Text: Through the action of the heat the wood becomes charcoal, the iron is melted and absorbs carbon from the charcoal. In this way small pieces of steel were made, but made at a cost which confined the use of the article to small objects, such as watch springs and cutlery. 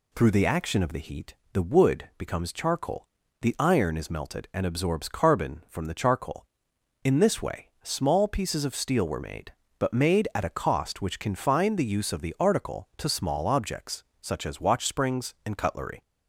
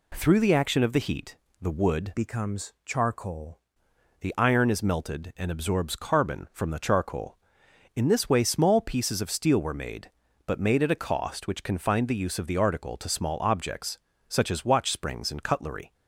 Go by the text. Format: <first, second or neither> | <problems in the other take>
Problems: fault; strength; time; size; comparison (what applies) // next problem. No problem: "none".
first | pauses between "heat" and "the"; slight; at 1.3 s; 0.26 s long; slight in the first // changes voice from "becomes" to "charcoal"; from 2.1 to 3.6 s; 1.5 s long